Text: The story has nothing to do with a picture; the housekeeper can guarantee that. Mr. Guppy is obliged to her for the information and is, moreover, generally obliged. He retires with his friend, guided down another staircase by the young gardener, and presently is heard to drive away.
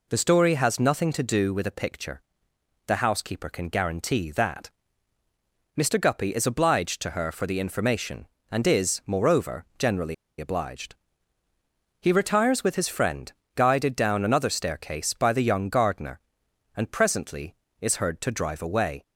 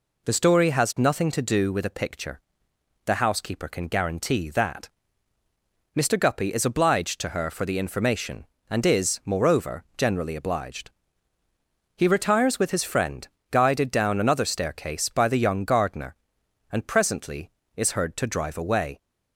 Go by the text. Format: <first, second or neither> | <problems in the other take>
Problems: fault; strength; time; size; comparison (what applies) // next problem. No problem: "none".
second | pauses between "generally" and "obliged"; slight; at 10.1 s; 0.24 s long